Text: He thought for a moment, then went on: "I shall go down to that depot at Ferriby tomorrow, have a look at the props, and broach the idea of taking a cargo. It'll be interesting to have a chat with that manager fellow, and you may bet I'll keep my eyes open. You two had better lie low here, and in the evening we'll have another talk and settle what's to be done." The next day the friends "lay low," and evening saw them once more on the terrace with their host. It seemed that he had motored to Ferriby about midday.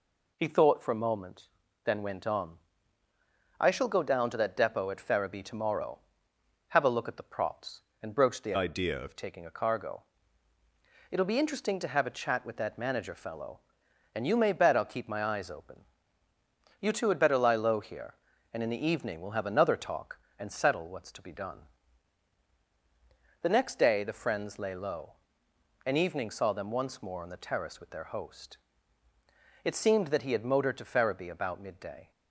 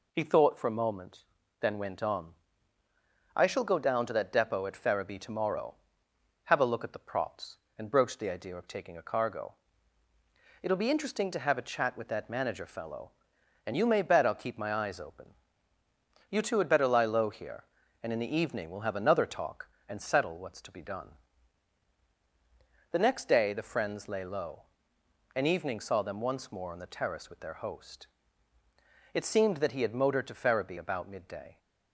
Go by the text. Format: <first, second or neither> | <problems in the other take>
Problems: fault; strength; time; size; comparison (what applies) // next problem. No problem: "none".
second | changes voice from "idea" to "of"; from 8.5 to 9.1 s; 0.6 s long